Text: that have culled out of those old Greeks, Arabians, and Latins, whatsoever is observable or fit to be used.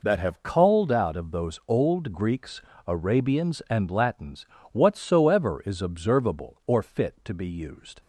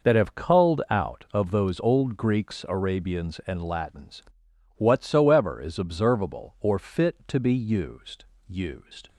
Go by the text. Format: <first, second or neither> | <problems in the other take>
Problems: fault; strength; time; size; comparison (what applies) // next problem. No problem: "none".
first | says "used" twice; at 8.4 s